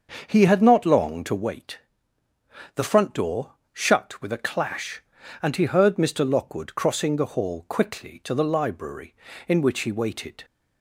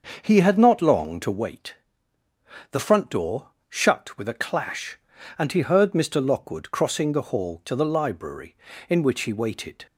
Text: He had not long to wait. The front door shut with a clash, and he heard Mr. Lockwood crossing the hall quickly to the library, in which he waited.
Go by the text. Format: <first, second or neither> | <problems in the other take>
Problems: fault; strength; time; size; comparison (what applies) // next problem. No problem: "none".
first | starts louder than the rest; until 1.2 s; 6.5 dB; also in the first // pauses between "door" and "shut"; slight; at 3.4 s; 0.22 s long; slight in the first // skips "quickly"; at 7.6 s